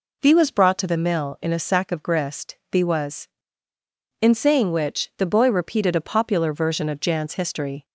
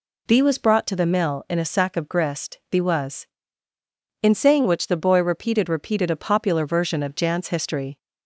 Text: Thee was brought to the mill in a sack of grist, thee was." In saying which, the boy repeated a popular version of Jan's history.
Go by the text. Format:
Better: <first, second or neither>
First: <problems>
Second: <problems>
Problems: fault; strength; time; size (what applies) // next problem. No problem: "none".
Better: first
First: none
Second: says "repeated" twice; at 5.6 s